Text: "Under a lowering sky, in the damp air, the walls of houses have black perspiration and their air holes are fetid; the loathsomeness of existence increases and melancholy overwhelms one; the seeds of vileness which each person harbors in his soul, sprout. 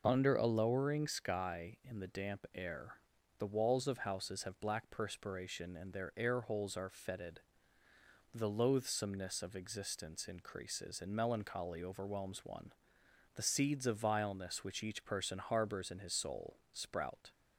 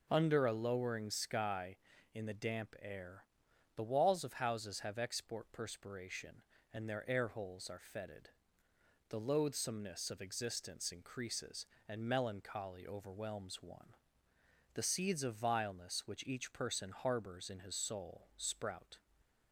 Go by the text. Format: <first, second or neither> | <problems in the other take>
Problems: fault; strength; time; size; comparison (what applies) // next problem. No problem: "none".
first | says "export" for "black"; at 4.9 s